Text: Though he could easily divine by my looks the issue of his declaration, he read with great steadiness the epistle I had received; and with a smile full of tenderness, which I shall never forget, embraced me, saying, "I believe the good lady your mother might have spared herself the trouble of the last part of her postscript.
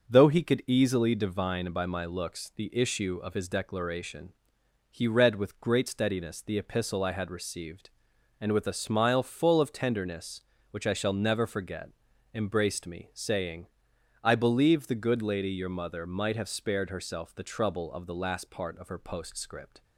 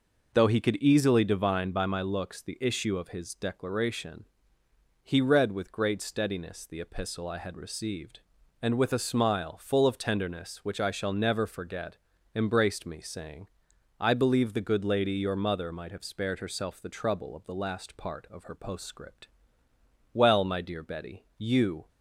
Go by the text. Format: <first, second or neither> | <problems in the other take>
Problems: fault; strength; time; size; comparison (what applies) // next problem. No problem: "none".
first | goes on to say "Well my dear Betty you"; strong; from 20.1 s on; 1.7 s long